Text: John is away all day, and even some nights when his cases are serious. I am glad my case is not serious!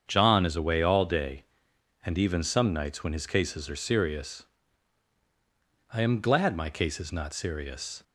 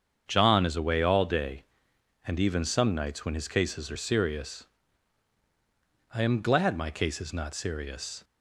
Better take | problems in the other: neither | starts louder than the rest; strong; the same in both

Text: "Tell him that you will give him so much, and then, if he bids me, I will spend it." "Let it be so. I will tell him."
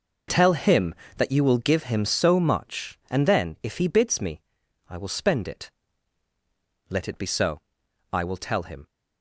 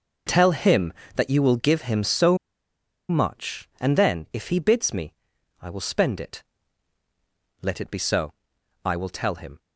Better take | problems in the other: first | pauses between "so" and "much"; noticeable; at 2.3 s; 0.71 s long

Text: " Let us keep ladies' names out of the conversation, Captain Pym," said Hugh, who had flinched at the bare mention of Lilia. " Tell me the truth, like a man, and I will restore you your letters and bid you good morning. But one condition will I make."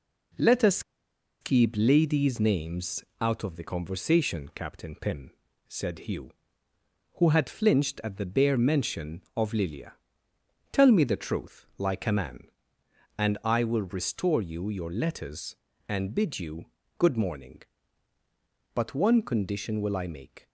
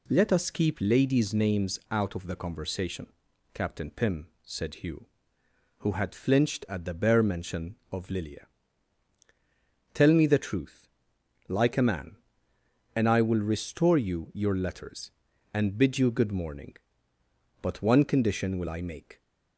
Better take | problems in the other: second | pauses between "us" and "keep"; noticeable; at 0.8 s; 0.60 s long // pauses between "names" and "out"; slight; at 3.0 s; 0.16 s long // pauses between "you" and "good"; slight; at 16.6 s; 0.34 s long

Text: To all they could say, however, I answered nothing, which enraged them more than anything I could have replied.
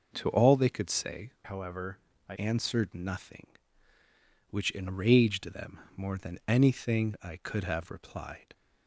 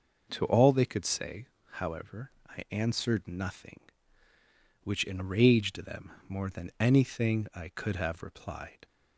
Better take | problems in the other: second | changes voice from "however" to "I"; from 1.4 to 2.3 s; 0.9 s long // pauses between "them" and "more"; slight; at 5.7 s; 0.16 s long; slight in the second

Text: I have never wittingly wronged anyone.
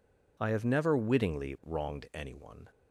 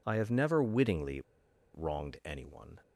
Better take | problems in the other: first | pauses between "wittingly" and "wronged"; noticeable; at 1.2 s; 0.52 s long

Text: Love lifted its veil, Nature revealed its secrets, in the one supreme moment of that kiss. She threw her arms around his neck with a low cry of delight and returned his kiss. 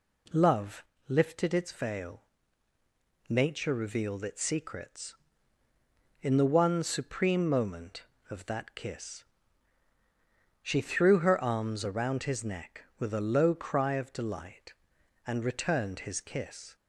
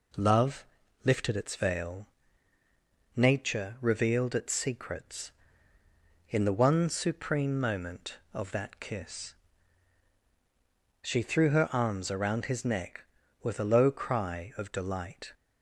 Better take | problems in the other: first | pauses between "Love" and "lifted"; at 0.6 s; 0.40 s long; slight in the first // stops before "and returned his kiss"; at 15.3 s

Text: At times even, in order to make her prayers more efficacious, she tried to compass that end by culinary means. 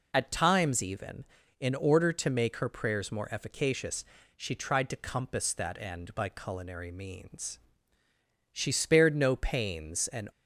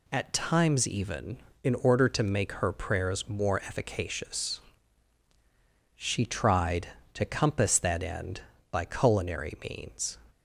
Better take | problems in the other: second | goes on to say "She spared no pains and"; strong; from 8.5 s on; 1.7 s long

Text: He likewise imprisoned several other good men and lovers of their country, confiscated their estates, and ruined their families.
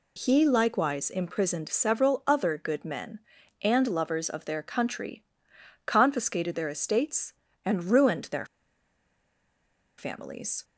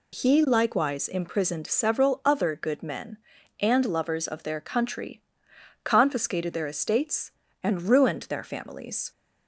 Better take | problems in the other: second | pauses between "their" and "families"; strong; at 8.4 s; 1.5 s long

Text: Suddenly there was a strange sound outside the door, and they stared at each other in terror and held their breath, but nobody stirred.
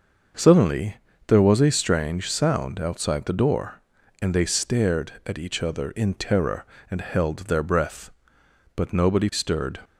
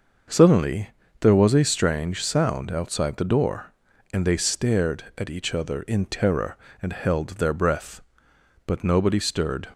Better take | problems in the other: neither | starts louder than the rest; the same in both // pauses between "Suddenly" and "there"; slight; the same in both

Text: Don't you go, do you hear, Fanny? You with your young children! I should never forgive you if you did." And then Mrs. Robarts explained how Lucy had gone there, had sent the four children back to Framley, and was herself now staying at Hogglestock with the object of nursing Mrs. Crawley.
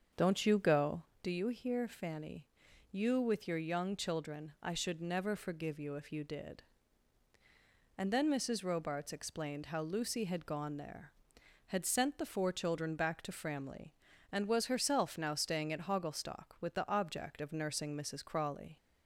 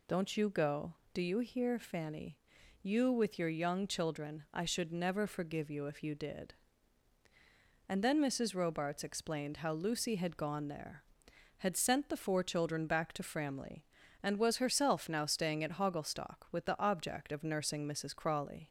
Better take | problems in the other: second | starts louder than the rest; until 1.1 s; 6.5 dB

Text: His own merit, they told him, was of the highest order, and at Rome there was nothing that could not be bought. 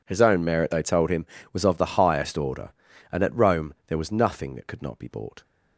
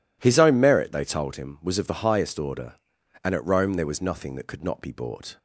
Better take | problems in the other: neither | none

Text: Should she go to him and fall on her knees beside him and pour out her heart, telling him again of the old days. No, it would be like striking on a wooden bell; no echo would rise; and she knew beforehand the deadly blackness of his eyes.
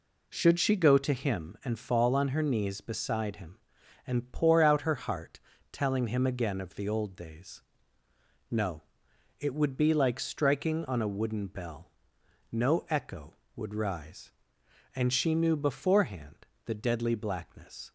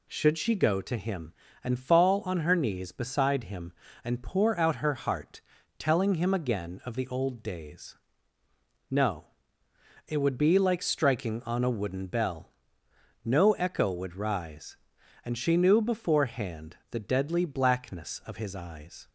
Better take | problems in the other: second | pauses between "beforehand" and "the"; slight; at 16.4 s; 0.20 s long // stops before "of his eyes"; at 17.8 s

